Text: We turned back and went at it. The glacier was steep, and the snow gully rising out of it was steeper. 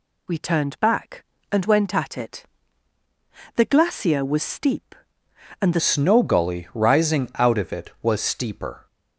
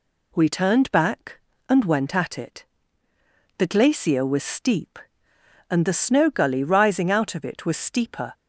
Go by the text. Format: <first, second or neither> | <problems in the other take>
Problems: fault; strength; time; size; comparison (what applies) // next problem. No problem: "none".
second | changes voice at "snow"; from 5.7 s on; 3.1 s long